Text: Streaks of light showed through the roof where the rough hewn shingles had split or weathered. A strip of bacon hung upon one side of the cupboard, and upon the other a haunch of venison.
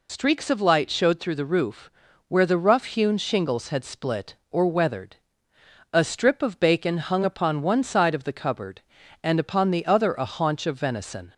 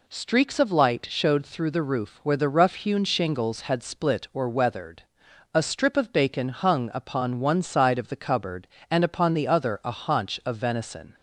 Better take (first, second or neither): second